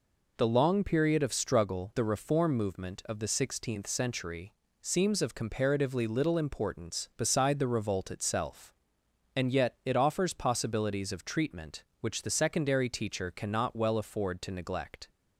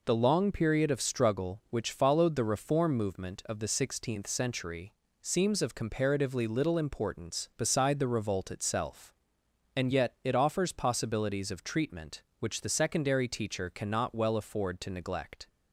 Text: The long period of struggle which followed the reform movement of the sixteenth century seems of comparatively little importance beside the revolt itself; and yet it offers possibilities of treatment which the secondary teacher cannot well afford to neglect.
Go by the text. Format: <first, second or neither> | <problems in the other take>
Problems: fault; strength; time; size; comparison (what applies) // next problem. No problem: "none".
second | skips "which followed"; at 1.9 s // pauses between "century" and "seems"; slight; at 4.5 s; 0.28 s long; slight in the second